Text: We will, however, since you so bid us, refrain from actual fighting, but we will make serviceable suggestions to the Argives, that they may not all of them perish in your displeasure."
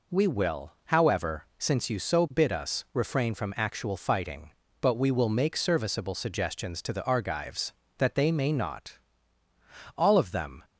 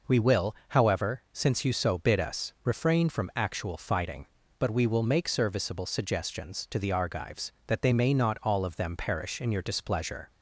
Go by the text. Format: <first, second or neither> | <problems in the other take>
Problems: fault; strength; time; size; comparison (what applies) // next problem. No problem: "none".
second | pauses between "not" and "all"; noticeable; at 8.9 s; 0.98 s long // stops before "perish in your displeasure"; at 10.6 s